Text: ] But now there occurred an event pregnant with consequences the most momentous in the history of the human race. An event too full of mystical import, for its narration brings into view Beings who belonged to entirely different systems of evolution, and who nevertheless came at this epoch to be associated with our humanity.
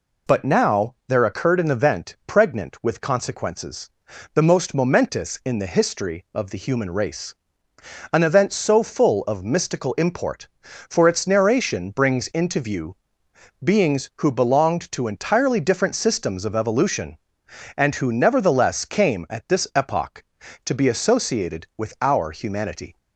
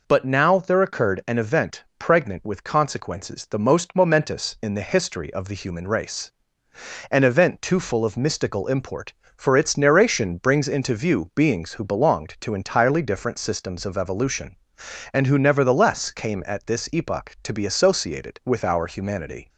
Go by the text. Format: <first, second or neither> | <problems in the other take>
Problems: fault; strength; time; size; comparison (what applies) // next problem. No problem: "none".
second | pauses between "consequences" and "the"; at 3.8 s; 0.44 s long // says "so" for "too"; at 8.5 s // pauses between "view" and "Beings"; noticeable; at 12.9 s; 0.66 s long